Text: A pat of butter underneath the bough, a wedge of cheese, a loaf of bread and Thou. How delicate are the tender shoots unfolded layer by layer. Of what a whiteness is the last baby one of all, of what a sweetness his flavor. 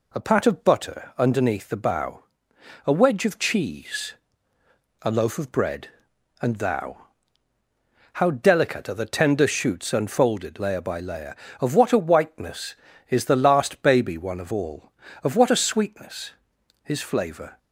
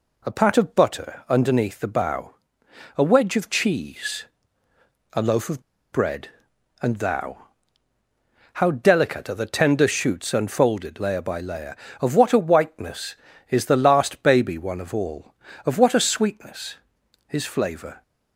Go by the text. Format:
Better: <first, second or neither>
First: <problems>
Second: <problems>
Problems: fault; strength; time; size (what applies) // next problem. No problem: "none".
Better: first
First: pauses between "sweetness" and "his"; noticeable; at 16.3 s; 0.52 s long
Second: pauses between "of" and "bread"; slight; at 5.6 s; 0.31 s long // pauses between "sweetness" and "his"; noticeable; at 16.7 s; 0.52 s long